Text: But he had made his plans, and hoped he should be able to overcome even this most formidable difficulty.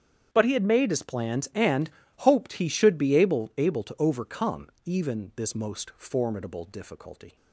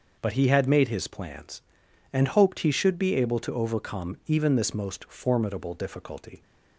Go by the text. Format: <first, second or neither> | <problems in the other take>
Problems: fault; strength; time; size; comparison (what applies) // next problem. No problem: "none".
second | starts louder than the rest; strong; until 1.3 s; 8.5 dB; noticeable in the second // pauses between "and" and "hoped"; slight; at 1.8 s; 0.30 s long // says "able" twice; at 3.5 s // pauses between "overcome" and "even"; slight; at 4.6 s; 0.16 s long